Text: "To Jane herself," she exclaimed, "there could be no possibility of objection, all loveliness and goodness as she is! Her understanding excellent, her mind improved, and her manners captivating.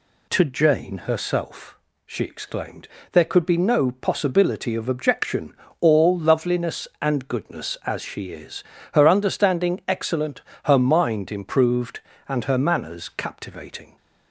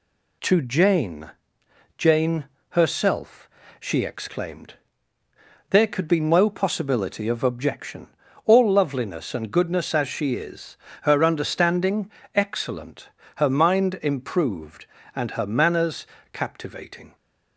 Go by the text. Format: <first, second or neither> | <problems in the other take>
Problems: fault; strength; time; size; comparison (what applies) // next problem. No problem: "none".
first | says "Jane" twice; at 1.9 s // pauses between "understanding" and "excellent"; slight; at 12.0 s; 0.26 s long // pauses between "manners" and "captivating"; slight; at 16.0 s; 0.24 s long